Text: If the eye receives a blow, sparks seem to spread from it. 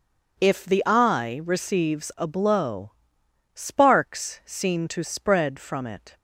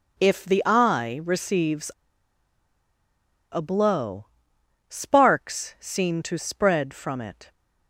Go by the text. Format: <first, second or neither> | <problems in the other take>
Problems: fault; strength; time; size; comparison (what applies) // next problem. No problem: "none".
first | pauses between "receives" and "a"; strong; at 1.9 s; 1.6 s long